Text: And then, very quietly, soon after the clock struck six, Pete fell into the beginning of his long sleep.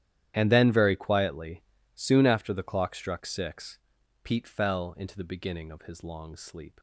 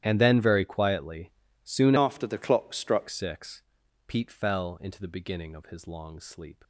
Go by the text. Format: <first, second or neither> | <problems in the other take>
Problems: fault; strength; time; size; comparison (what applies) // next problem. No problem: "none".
first | starts louder than the rest; strong; until 1.0 s; 11.5 dB; strong in the first // changes voice from "after" to "struck"; from 1.9 to 3.0 s; 1.1 s long